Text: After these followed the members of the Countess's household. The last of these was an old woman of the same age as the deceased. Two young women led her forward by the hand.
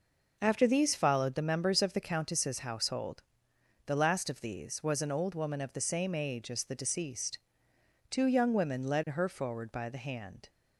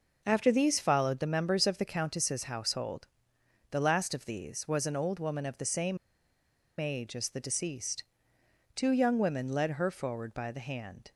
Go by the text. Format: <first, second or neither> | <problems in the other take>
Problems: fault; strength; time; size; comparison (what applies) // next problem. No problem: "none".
first | pauses between "same" and "age"; noticeable; at 5.9 s; 0.81 s long